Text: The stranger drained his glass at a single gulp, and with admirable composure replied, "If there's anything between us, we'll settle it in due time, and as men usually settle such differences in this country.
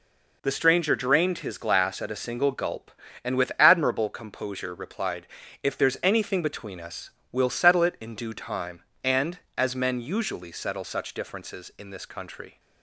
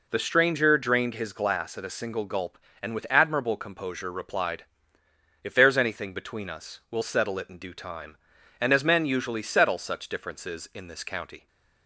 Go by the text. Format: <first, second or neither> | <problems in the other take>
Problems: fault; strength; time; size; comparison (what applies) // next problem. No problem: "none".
first | says "county" for "country"; at 11.0 s